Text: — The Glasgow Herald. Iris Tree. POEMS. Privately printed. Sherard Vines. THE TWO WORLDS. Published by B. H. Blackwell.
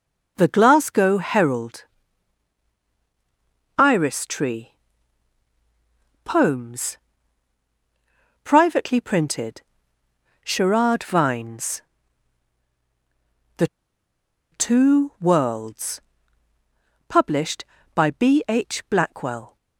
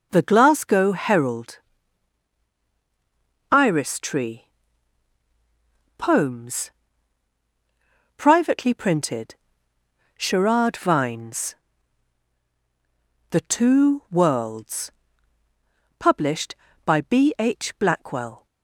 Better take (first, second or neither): second